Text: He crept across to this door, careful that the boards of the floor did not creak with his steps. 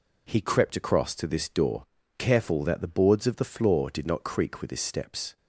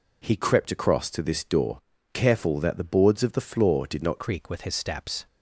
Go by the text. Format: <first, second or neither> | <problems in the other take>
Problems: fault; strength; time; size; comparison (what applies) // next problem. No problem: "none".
first | changes voice at "creak"; from 4.1 s on; 1.1 s long